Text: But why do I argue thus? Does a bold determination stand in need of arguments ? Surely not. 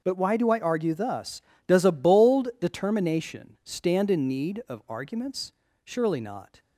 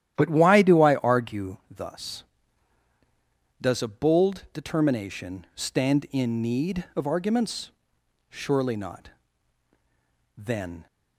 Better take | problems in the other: first | starts louder than the rest; strong; until 1.1 s; 11.5 dB // goes on to say "Then"; from 10.3 s on; 0.50 s long

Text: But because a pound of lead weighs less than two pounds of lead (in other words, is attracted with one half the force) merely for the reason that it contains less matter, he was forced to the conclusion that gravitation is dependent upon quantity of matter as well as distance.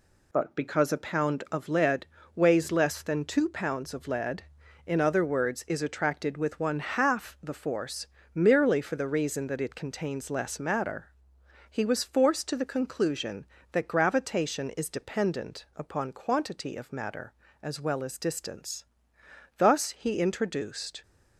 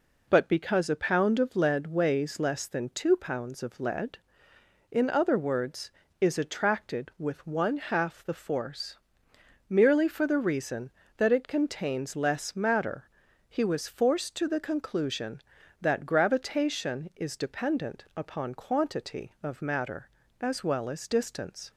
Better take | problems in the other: second | pauses between "lead" and "weighs"; slight; at 2.0 s; 0.28 s long // goes on to say "Thus he introduced"; from 19.5 s on; 1.4 s long

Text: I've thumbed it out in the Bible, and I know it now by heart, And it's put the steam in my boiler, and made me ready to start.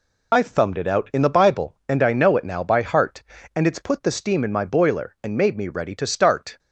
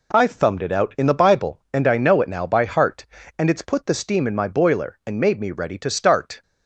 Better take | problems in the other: second | loses the start of "I've"; at 0.3 s; 65 ms

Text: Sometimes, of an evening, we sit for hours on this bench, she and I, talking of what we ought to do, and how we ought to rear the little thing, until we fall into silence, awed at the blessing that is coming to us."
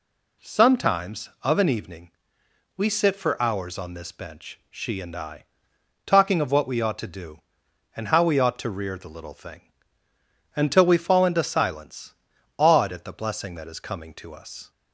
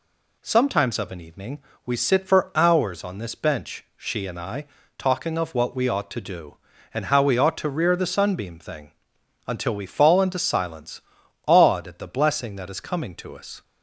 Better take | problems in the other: first | says "sunbeam" for "little"; at 8.0 s

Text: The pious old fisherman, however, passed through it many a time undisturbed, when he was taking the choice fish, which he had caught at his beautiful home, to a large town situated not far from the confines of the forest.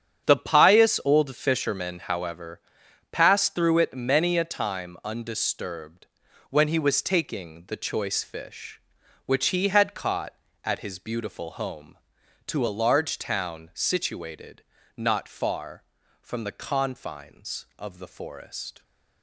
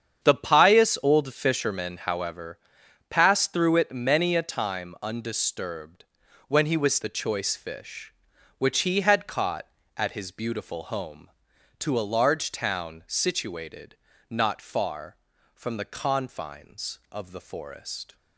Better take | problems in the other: first | starts louder than the rest; strong; until 1.2 s; 8 dB; strong in the first // skips "taking"; at 7.0 s // pauses between "situated" and "not"; slight; at 13.9 s; 0.32 s long; slight in the first

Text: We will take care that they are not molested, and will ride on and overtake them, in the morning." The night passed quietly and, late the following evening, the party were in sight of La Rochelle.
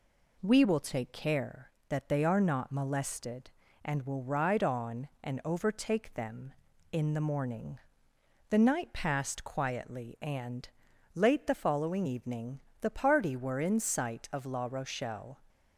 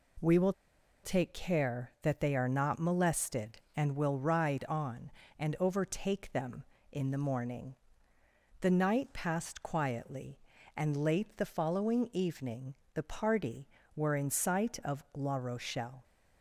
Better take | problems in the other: first | pauses between "will" and "take"; noticeable; at 0.5 s; 0.51 s long

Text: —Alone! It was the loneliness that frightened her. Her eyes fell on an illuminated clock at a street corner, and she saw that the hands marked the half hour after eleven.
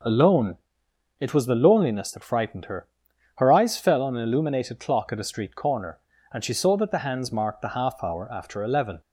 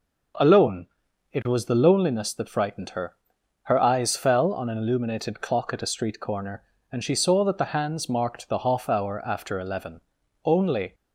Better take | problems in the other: first | goes on to say "Only"; from 10.4 s on; 0.50 s long

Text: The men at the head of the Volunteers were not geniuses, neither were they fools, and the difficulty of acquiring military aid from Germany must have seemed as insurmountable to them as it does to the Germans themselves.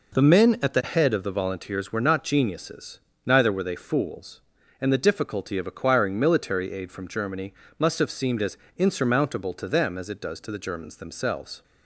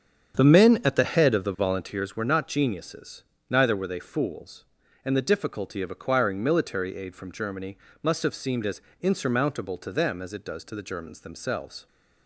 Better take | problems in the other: first | starts louder than the rest; strong; until 2.1 s; 7.5 dB // pauses between "Germany" and "must"; slight; at 7.7 s; 0.26 s long; slight in the first // pauses between "as" and "insurmountable"; slight; at 8.8 s; 0.20 s long; slight in the first

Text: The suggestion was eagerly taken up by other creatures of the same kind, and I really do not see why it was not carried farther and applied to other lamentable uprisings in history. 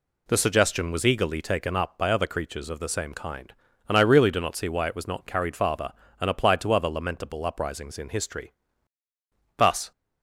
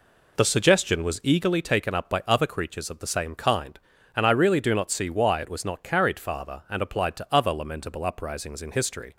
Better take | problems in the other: second | goes on to say "Thus"; slight; from 9.5 s on; 0.34 s long

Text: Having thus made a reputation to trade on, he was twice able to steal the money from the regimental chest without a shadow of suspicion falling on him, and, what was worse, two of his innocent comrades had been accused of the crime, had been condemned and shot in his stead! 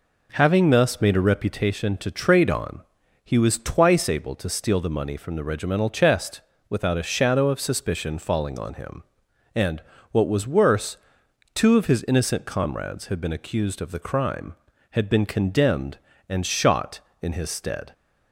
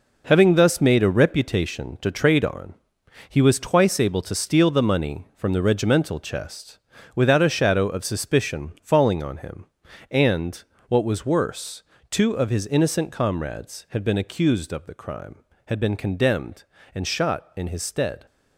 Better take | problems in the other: first | gets quieter; strong; throughout; 8.5 dB // pauses between "chest" and "without"; slight; at 6.7 s; 0.34 s long; slight in the first

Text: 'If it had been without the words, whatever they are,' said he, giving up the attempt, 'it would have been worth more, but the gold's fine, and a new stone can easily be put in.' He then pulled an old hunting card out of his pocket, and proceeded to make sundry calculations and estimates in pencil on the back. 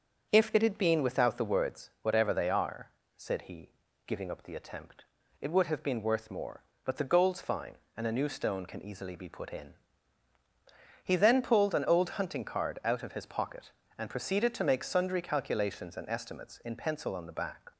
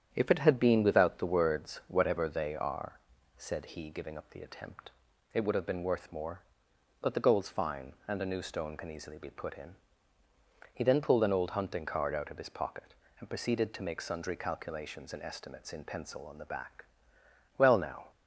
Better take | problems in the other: first | starts louder than the rest; strong; until 1.1 s; 9 dB; also in the first // goes on to say "Well now"; from 17.5 s on; 0.54 s long

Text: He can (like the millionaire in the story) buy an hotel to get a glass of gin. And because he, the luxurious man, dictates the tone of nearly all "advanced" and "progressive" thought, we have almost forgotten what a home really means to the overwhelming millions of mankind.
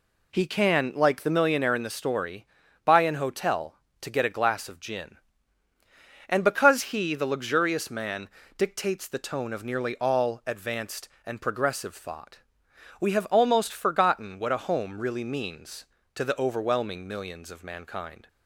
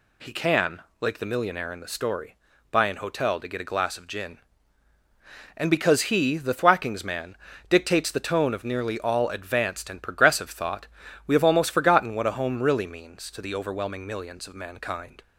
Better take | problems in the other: first | says "thwackings" for "luxurious"; at 6.5 s

